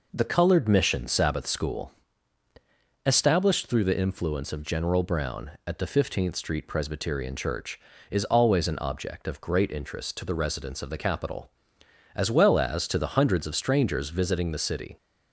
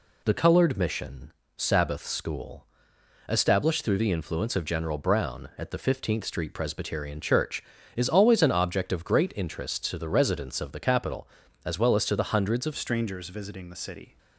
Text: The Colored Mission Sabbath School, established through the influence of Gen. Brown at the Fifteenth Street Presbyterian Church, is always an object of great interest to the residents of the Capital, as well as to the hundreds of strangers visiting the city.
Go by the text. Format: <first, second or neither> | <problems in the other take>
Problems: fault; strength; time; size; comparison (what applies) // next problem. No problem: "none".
first | pauses between "Mission" and "Sabbath"; slight; at 1.3 s; 0.26 s long // changes voice at "strangers"; from 12.7 s on; 1.4 s long